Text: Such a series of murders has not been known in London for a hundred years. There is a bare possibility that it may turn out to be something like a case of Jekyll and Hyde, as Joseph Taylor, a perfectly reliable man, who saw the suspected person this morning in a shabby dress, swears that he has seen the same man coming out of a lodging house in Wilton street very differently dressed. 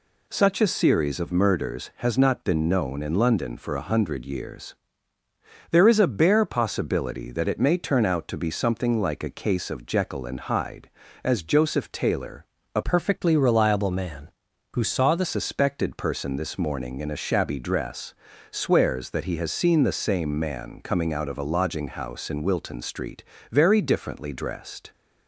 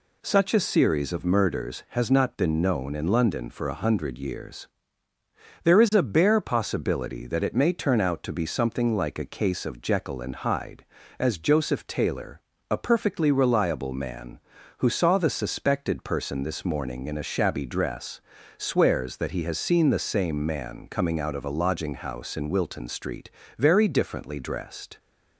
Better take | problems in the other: second | changes voice from "perfectly" to "the"; from 12.8 to 15.2 s; 2.4 s long // pauses between "street" and "very"; slight; at 23.2 s; 0.30 s long; slight in the second

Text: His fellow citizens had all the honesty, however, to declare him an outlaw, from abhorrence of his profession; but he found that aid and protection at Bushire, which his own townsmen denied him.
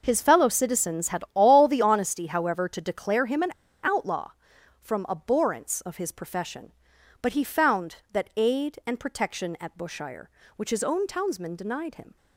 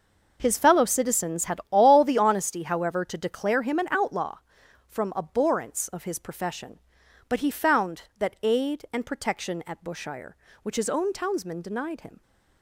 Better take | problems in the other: second | pauses between "an" and "outlaw"; slight; at 3.5 s; 0.33 s long

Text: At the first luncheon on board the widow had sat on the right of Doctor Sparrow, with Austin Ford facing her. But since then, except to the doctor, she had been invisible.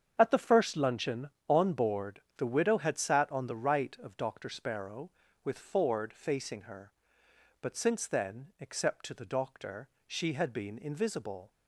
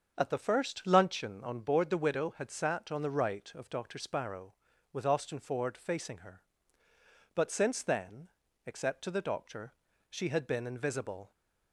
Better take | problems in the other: second | starts louder than the rest; strong; until 1.1 s; 8 dB; also in the second // pauses between "board" and "the"; slight; at 2.2 s; 0.16 s long // skips "Austin"; at 5.5 s

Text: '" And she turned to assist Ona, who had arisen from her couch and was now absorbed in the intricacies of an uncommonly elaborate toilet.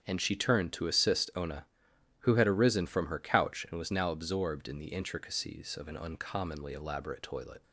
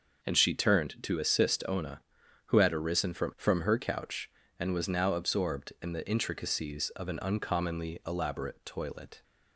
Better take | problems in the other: first | starts louder than the rest; noticeable; until 1.2 s; 6 dB; strong in the first // says "from" twice; at 3.3 s

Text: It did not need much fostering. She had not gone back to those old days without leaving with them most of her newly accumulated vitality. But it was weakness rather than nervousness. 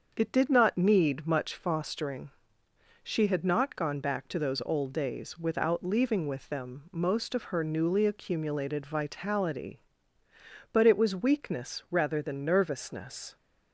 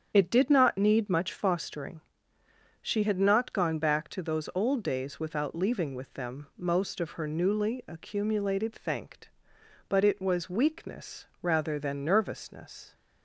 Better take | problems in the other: first | starts louder than the rest; strong; until 1.1 s; 7.5 dB; also in the first // says "thanked" for "vitality"; at 8.7 s // pauses between "weakness" and "rather"; slight; at 11.2 s; 0.16 s long

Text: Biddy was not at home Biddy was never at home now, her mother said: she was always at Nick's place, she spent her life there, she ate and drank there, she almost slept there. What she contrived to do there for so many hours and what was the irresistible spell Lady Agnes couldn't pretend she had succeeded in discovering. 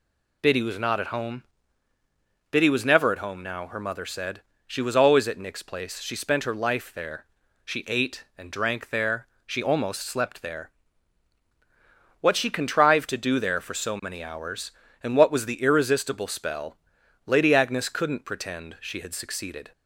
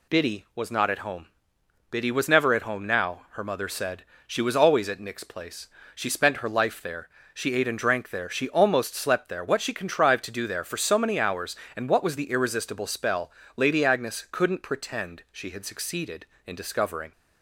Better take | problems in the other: second | pauses between "home" and "Biddy"; at 1.4 s; 1.0 s long; noticeable in the second // pauses between "spell" and "Lady"; noticeable; at 16.7 s; 0.48 s long; slight in the second // stops before "in discovering"; at 19.7 s

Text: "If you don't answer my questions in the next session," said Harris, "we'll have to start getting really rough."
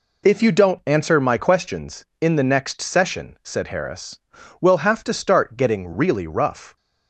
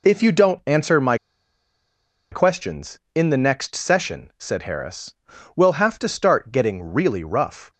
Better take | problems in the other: first | pauses between "my" and "questions"; at 1.1 s; 1.1 s long

